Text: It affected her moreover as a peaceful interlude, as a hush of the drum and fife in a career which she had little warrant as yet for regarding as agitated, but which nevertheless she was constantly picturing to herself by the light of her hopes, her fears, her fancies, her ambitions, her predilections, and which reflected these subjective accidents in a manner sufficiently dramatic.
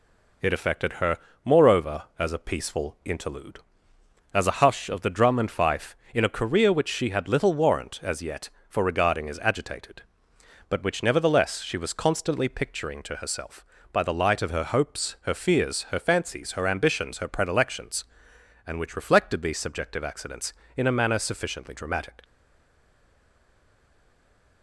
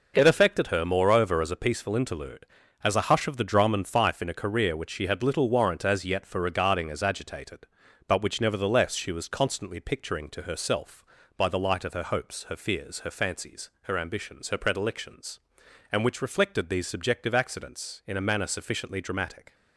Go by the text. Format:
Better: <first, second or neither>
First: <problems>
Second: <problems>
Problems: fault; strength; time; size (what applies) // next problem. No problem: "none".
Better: second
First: pauses between "her" and "moreover"; slight; at 1.1 s; 0.26 s long // stays silent after the last word; from 22.2 s on; 2.4 s long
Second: none